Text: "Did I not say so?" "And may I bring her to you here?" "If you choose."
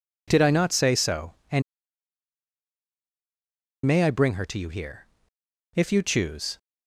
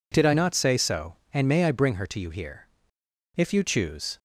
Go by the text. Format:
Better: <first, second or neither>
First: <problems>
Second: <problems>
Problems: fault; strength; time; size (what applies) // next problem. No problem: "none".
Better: second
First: pauses between "And" and "may"; strong; at 1.6 s; 2.2 s long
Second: none